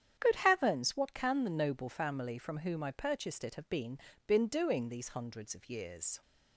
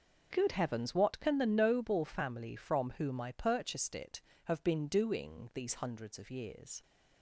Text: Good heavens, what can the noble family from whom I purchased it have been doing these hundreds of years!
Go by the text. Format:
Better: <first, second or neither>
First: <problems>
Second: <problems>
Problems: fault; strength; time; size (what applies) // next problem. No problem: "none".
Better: second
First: starts louder than the rest; strong; until 1.2 s; 9 dB // says "been" twice; at 4.2 s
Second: starts louder than the rest; noticeable; until 1.3 s; 6 dB